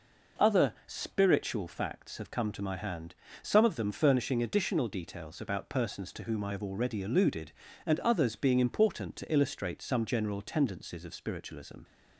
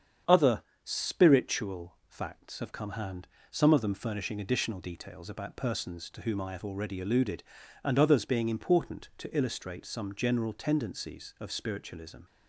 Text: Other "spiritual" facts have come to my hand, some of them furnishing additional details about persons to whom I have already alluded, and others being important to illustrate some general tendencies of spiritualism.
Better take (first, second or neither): first